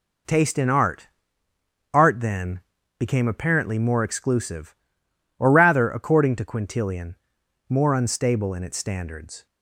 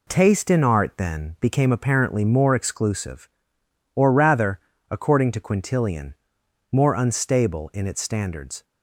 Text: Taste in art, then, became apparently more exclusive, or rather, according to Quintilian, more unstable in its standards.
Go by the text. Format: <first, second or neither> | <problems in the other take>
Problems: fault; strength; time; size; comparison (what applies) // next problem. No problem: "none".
second | says "art" twice; at 1.9 s